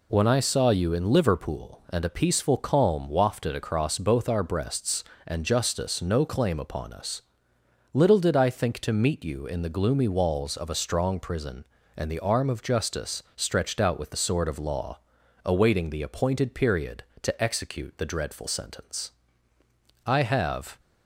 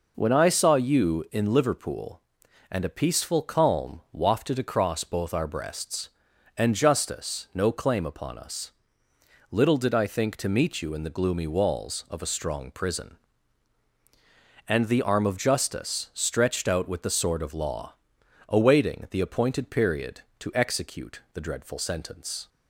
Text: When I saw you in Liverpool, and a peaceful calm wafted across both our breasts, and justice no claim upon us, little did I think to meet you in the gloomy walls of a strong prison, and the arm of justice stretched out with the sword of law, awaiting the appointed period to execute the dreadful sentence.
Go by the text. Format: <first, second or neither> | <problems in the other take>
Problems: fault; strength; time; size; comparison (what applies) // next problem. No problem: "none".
second | goes on to say "I have"; noticeable; from 20.0 s on; 0.72 s long